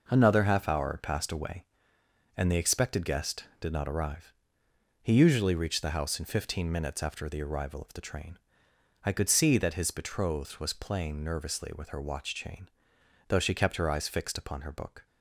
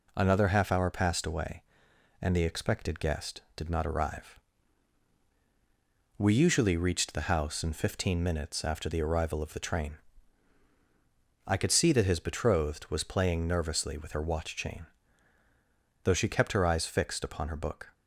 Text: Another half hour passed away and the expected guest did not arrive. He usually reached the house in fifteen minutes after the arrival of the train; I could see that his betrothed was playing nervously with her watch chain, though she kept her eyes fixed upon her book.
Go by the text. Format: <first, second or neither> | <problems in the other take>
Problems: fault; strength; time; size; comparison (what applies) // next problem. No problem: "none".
first | says "We" for "He"; at 6.1 s